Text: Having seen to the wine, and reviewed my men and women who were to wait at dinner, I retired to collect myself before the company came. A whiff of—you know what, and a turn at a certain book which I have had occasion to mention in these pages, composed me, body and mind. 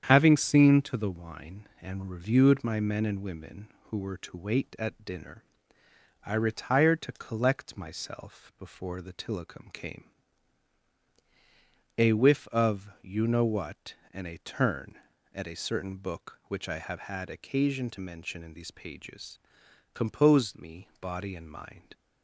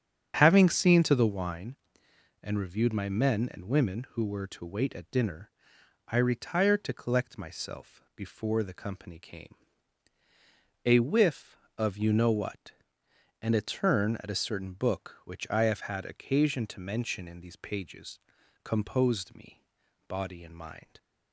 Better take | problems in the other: second | starts louder than the rest; strong; until 1.0 s; 8.5 dB; strong in the second // says "tillicum" for "company"; at 9.1 s

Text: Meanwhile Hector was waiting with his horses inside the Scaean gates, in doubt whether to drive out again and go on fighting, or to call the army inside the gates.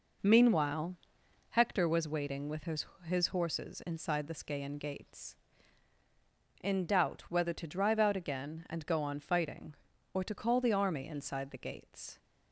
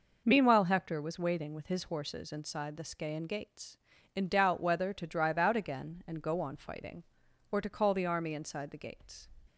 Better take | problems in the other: second | pauses between "Meanwhile" and "Hector"; noticeable; at 0.9 s; 0.54 s long // says "his" twice; at 3.0 s

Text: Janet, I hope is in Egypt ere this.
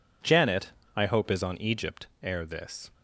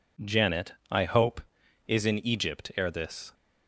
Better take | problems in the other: second | says "on" for "in"; at 1.4 s // pauses between "Egypt" and "ere"; slight; at 2.0 s; 0.16 s long

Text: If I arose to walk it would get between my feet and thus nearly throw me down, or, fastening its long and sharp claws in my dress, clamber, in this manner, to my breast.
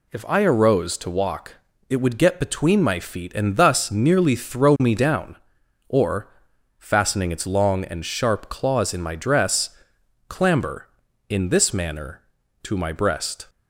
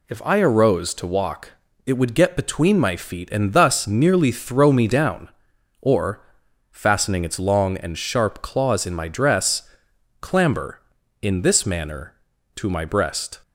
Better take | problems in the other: neither | pauses between "walk" and "it"; slight; the same in both

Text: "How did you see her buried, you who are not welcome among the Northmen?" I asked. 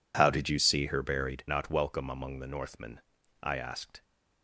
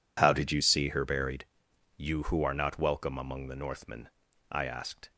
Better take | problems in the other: second | skips "you who are"; at 1.4 s

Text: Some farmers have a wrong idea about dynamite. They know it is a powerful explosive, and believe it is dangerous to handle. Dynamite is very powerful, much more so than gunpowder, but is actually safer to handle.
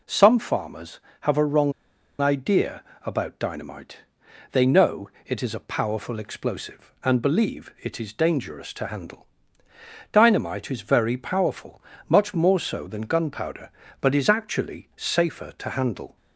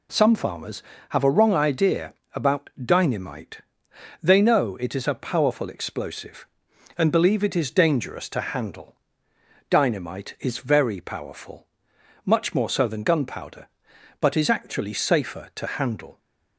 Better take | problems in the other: second | pauses between "wrong" and "idea"; noticeable; at 1.7 s; 0.49 s long // pauses between "idea" and "about"; slight; at 2.8 s; 0.24 s long; slight in the second // pauses between "know" and "it"; slight; at 5.0 s; 0.18 s long

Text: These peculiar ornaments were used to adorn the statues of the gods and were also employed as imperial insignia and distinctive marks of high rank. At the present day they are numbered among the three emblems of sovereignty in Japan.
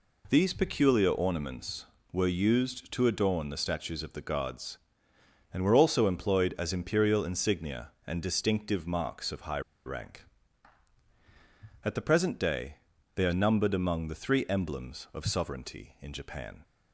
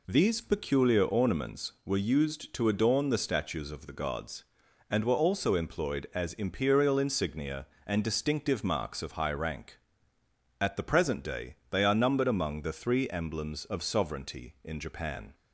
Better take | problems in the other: second | pauses between "high" and "rank"; slight; at 9.5 s; 0.25 s long // pauses between "day" and "they"; at 12.7 s; 0.38 s long

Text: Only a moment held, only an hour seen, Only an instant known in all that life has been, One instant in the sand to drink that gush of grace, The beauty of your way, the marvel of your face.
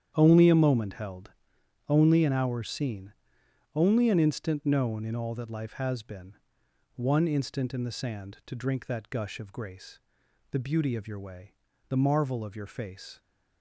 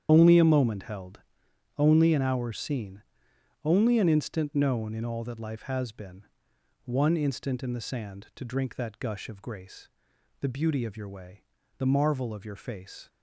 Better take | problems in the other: first | loses the start of "Only"; at 0.0 s; 50 ms // starts louder than the rest; strong; until 1.1 s; 9 dB; strong in the first

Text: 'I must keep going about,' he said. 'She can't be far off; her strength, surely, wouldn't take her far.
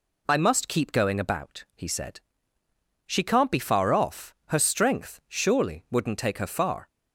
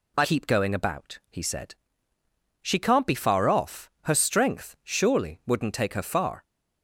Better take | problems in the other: first | skips "must"; at 0.2 s

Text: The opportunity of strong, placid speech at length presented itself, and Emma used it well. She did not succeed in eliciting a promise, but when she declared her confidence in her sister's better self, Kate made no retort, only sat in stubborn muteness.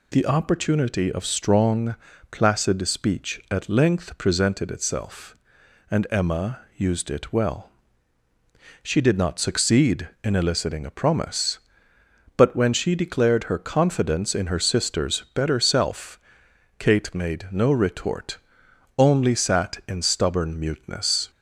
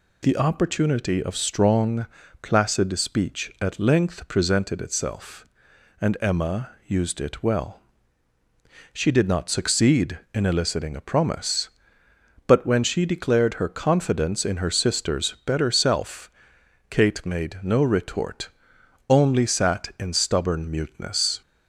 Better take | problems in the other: neither | pauses between "Emma" and "used"; slight; the same in both

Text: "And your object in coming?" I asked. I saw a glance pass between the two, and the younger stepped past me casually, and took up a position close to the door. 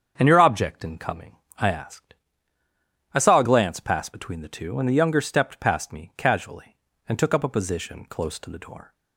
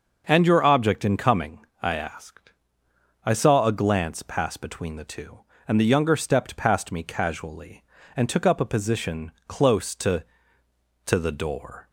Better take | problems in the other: first | starts louder than the rest; noticeable; until 1.2 s; 6 dB; strong in the first // pauses between "position" and "close"; slight; at 9.3 s; 0.18 s long // says "to" twice; at 11.0 s

